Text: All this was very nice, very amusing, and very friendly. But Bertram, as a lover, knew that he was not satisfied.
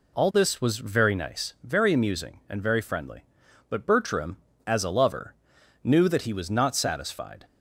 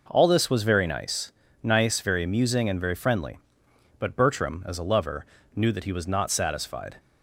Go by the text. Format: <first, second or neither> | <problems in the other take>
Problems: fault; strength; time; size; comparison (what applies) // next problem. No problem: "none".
first | says "nice" twice; at 1.6 s